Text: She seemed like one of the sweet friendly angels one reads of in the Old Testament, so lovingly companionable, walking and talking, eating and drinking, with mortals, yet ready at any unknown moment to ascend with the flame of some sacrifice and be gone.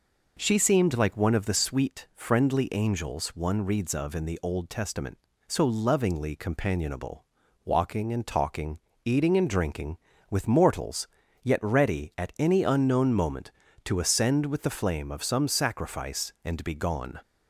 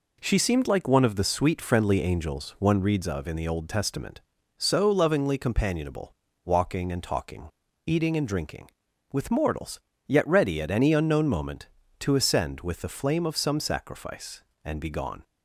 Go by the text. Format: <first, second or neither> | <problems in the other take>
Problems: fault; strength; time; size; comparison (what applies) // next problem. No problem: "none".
neither | none